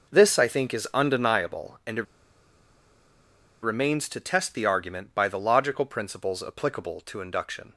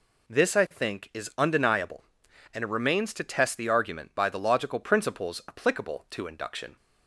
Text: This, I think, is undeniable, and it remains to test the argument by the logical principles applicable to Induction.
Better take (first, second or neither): second